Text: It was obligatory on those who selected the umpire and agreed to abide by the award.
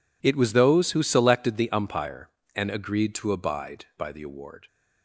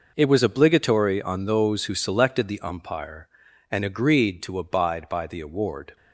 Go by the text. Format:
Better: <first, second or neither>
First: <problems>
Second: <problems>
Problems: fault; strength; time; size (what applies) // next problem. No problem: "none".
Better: second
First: skips "obligatory on"; at 0.5 s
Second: none